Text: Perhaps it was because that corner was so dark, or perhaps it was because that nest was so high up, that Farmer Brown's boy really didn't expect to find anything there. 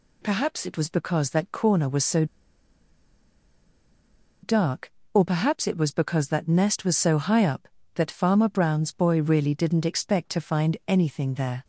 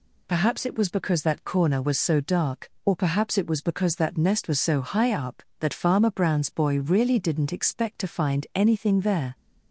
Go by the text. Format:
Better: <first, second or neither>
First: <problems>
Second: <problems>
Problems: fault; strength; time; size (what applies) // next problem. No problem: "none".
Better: second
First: pauses between "so" and "dark"; strong; at 2.2 s; 2.1 s long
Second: none